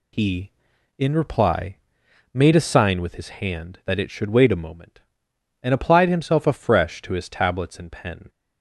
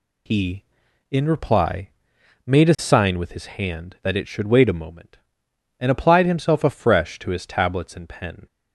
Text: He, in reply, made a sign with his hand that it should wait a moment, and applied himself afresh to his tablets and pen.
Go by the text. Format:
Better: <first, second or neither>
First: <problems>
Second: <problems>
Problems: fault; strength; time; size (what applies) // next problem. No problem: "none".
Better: neither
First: none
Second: none